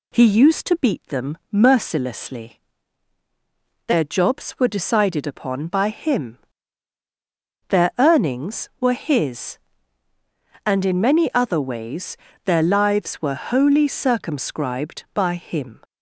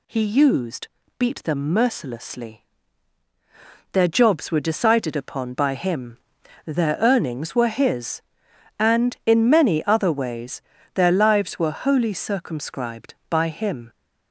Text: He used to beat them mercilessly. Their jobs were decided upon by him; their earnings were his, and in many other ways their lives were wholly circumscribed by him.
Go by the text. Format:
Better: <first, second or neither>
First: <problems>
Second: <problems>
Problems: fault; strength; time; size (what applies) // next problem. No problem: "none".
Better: first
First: pauses between "ways" and "their"; slight; at 12.1 s; 0.30 s long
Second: skips "to"; at 1.0 s // pauses between "ways" and "their"; slight; at 10.6 s; 0.32 s long